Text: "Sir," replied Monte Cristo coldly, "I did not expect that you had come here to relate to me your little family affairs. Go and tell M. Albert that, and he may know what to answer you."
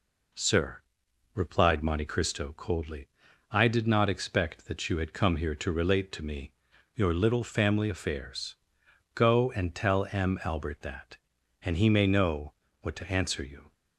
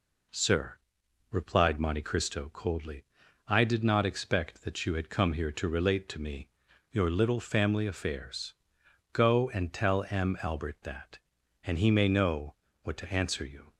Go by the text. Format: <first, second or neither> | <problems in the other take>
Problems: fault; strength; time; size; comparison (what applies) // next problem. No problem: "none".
neither | pauses between "me" and "your"; the same in both // pauses between "know" and "what"; slight; the same in both